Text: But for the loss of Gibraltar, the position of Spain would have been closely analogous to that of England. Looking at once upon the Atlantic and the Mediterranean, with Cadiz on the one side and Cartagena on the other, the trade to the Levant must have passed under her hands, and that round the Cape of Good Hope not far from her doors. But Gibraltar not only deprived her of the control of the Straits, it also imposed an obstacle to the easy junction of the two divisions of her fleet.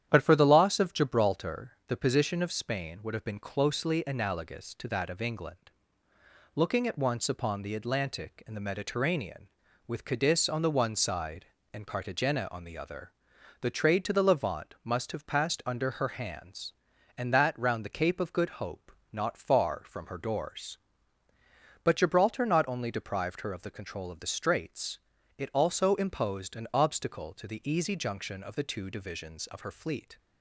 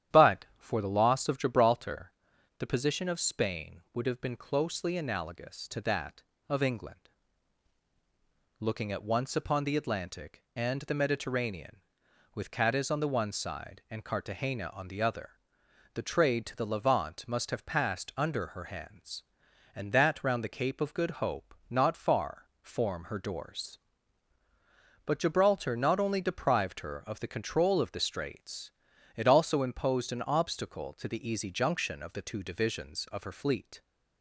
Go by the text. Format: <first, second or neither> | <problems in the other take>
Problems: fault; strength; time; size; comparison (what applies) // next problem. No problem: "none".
first | starts louder than the rest; strong; until 1.2 s; 10.5 dB; strong in the first // pauses between "Hope" and "not"; slight; at 21.5 s; 0.16 s long; slight in the first // says "form" for "from"; at 22.6 s